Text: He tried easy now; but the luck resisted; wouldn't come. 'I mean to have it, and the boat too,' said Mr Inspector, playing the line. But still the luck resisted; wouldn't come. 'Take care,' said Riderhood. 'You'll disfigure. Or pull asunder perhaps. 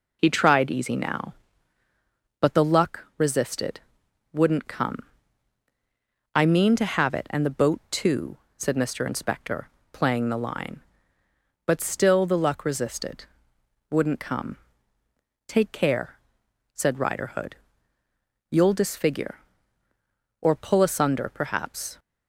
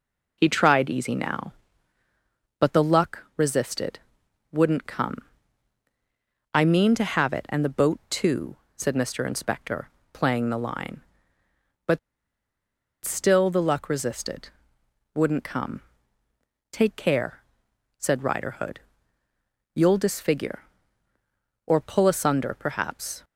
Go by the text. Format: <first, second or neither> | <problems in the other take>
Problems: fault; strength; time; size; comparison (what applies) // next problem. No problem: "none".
first | pauses between "But" and "still"; at 11.9 s; 1.0 s long